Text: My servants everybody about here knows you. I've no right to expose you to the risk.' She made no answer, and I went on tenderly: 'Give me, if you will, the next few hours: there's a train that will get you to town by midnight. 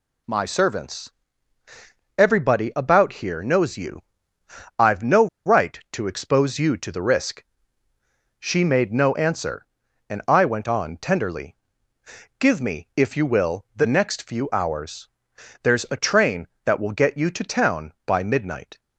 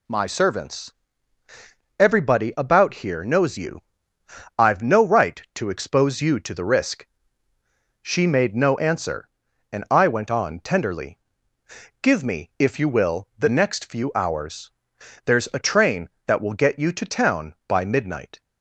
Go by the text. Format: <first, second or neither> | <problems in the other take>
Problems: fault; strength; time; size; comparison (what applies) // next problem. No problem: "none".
second | pauses between "servants" and "everybody"; at 1.0 s; 1.0 s long; also in the second // pauses between "no" and "right"; slight; at 5.2 s; 0.19 s long